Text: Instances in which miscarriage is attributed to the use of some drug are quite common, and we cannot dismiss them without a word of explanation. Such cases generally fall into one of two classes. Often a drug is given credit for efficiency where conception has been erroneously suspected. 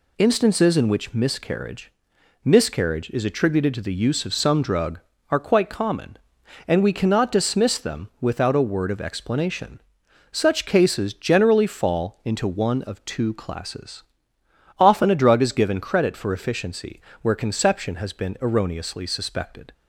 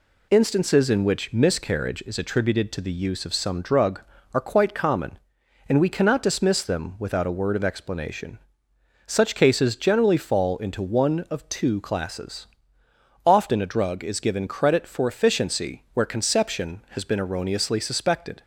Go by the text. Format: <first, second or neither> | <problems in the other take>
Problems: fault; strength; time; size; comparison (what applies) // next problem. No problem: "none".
second | says "miscarriage" twice; at 2.4 s // pauses between "efficiency" and "where"; slight; at 17.0 s; 0.20 s long